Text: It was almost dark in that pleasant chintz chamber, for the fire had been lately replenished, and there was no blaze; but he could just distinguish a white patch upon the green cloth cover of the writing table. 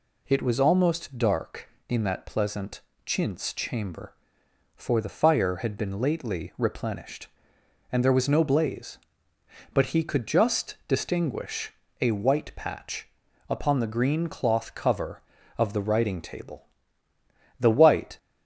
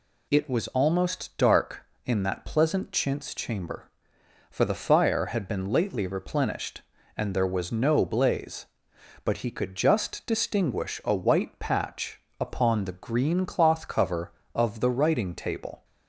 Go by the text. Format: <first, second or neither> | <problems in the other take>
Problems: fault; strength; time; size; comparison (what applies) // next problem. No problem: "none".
second | pauses between "pleasant" and "chintz"; slight; at 2.8 s; 0.24 s long // pauses between "distinguish" and "a"; slight; at 11.7 s; 0.30 s long // pauses between "patch" and "upon"; at 13.0 s; 0.40 s long; slight in the second // goes on to say "The white"; from 17.5 s on; 0.58 s long